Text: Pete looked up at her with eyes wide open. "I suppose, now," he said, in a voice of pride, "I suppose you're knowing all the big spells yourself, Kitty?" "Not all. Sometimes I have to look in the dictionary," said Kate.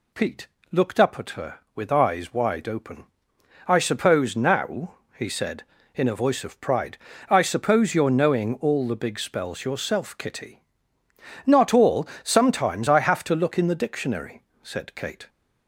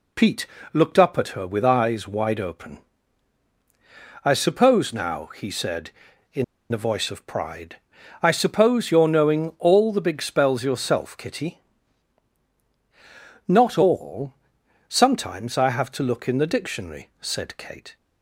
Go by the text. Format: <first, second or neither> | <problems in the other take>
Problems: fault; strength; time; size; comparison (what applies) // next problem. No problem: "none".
first | pauses between "Pete" and "looked"; slight; at 0.4 s; 0.26 s long; slight in the first // pauses between "in" and "a"; slight; at 6.4 s; 0.27 s long